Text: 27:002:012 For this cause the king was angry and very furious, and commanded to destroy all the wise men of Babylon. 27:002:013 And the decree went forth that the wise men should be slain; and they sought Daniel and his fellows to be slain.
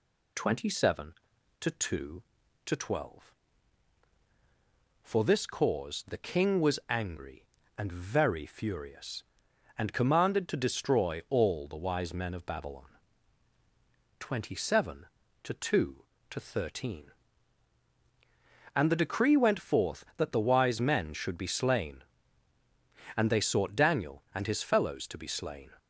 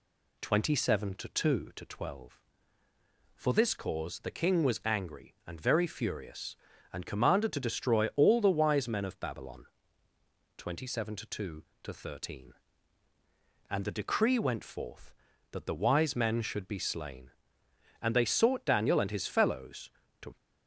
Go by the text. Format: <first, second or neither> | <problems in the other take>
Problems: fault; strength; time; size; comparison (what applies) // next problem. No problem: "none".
first | stops before "be slain"; at 20.3 s